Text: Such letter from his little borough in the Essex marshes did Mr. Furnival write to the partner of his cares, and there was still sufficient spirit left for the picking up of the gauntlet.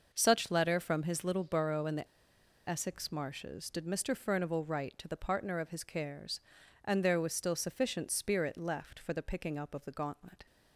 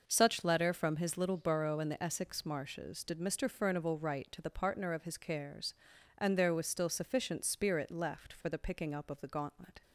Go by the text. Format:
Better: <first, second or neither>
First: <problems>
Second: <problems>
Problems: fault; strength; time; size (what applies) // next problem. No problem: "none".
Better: second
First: pauses between "the" and "Essex"; noticeable; at 2.0 s; 0.60 s long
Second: none